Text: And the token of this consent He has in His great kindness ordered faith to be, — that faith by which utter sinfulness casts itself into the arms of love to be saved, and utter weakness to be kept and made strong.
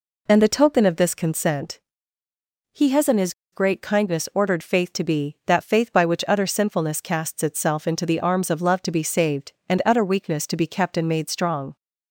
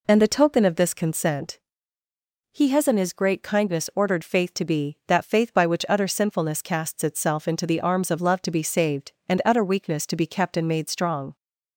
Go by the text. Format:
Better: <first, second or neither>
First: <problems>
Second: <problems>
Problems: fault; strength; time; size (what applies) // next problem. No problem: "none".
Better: second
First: pauses between "consent" and "He"; noticeable; at 1.7 s; 0.92 s long // pauses between "His" and "great"; slight; at 3.3 s; 0.20 s long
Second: pauses between "consent" and "He"; noticeable; at 1.5 s; 0.92 s long